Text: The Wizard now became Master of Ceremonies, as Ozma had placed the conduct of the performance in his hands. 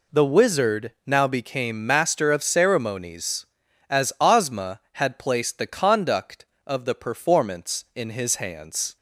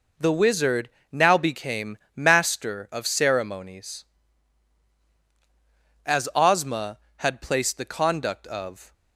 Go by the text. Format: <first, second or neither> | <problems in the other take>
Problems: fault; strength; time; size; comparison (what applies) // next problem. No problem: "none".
first | pauses between "Wizard" and "now"; slight; at 0.8 s; 0.22 s long // pauses between "became" and "Master"; slight; at 1.9 s; 0.18 s long // stops before "the performance in his hands"; at 8.9 s